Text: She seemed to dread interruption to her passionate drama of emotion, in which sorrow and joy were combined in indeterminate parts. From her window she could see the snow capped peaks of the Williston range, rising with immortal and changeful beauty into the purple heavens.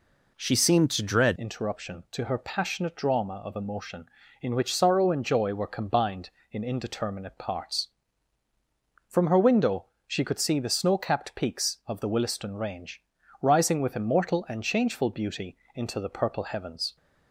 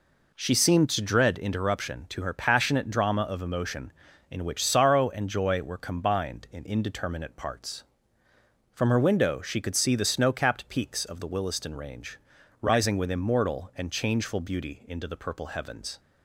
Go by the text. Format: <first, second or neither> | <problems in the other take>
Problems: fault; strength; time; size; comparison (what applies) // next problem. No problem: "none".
second | changes voice at "interruption"; from 1.3 s on; 15.6 s long // pauses between "window" and "she"; slight; at 9.8 s; 0.22 s long // pauses between "beauty" and "into"; slight; at 15.5 s; 0.16 s long